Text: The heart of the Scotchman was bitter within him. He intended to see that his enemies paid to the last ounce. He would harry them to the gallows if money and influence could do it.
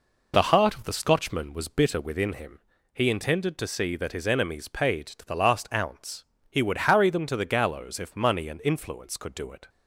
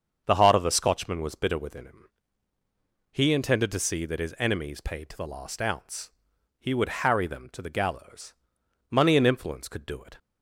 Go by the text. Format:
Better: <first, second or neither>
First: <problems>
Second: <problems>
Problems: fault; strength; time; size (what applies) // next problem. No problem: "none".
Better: first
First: none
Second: starts louder than the rest; until 1.2 s; 7 dB // skips "if"; at 8.6 s